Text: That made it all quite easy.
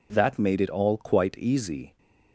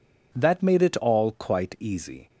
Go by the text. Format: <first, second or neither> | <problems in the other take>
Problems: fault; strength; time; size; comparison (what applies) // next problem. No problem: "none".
neither | none